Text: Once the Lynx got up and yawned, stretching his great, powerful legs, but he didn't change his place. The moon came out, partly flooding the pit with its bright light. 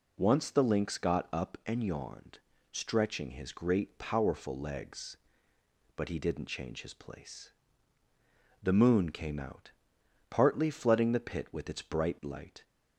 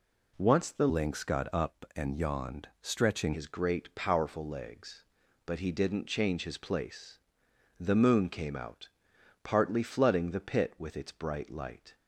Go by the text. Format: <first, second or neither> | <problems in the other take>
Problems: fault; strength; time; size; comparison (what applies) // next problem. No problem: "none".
first | changes voice from "Lynx" to "stretching"; from 0.8 to 3.3 s; 2.5 s long